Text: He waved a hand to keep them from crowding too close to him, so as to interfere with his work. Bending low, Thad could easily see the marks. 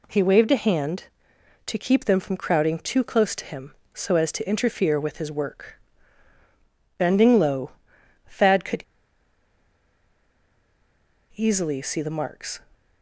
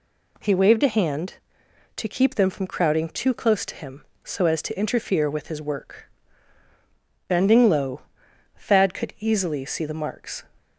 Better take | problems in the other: second | pauses between "could" and "easily"; strong; at 8.8 s; 2.5 s long

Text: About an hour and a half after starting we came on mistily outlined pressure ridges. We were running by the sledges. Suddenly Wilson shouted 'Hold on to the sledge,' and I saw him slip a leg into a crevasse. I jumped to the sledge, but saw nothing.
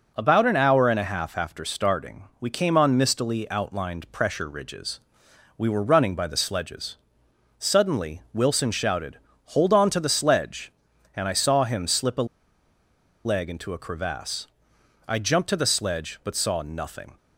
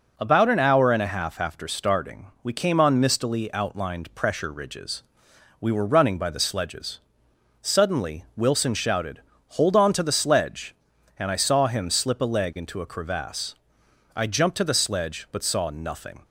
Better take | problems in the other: second | pauses between "shouted" and "Hold"; slight; at 9.1 s; 0.28 s long; slight in the second // pauses between "a" and "leg"; at 12.2 s; 0.98 s long

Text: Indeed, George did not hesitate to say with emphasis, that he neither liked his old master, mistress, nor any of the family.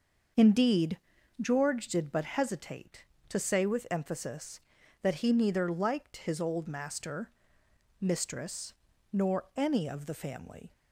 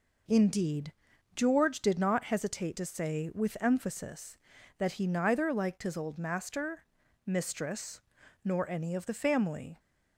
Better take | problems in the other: second | starts louder than the rest; noticeable; until 1.8 s; 6 dB // says "but" for "not"; at 2.1 s

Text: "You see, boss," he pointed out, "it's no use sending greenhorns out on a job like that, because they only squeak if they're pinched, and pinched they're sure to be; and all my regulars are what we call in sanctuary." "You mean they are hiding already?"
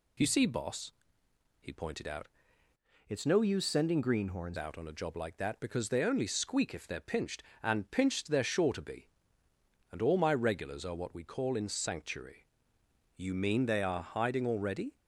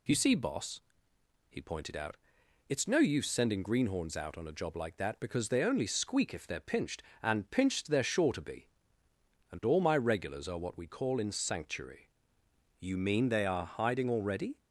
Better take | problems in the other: second | changes voice from "it's" to "greenhorns"; from 3.0 to 4.5 s; 1.5 s long

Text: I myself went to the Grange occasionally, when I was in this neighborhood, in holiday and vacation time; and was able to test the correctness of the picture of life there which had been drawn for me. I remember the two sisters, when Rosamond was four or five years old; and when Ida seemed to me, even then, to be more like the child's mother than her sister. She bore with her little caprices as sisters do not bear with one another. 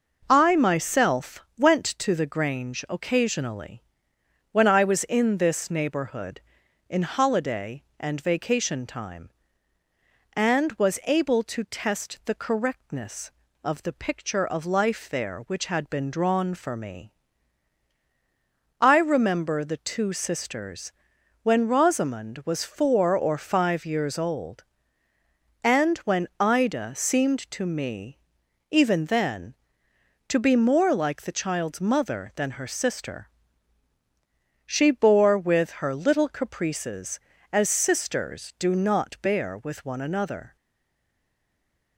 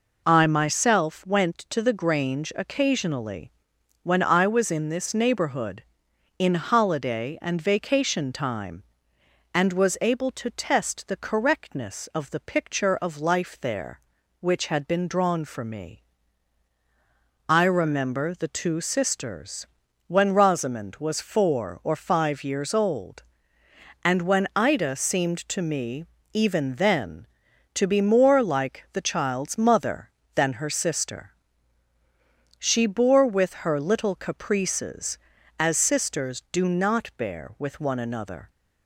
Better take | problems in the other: second | pauses between "myself" and "went"; slight; at 1.4 s; 0.16 s long // stays silent after the last word; noticeable; from 40.5 s on; 1.4 s long

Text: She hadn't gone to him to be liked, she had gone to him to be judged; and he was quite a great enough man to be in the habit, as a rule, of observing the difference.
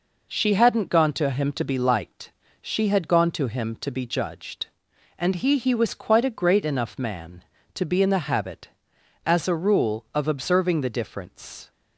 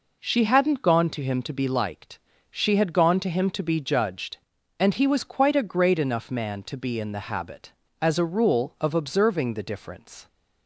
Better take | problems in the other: second | says "he" twice; at 5.5 s

